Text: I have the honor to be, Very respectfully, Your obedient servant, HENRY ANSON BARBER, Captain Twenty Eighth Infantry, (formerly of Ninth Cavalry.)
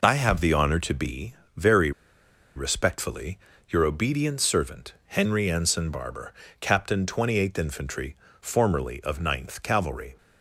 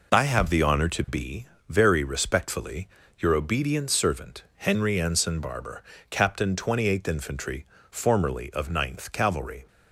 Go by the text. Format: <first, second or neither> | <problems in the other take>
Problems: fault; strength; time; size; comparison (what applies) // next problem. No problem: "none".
second | pauses between "Very" and "respectfully"; noticeable; at 1.9 s; 0.65 s long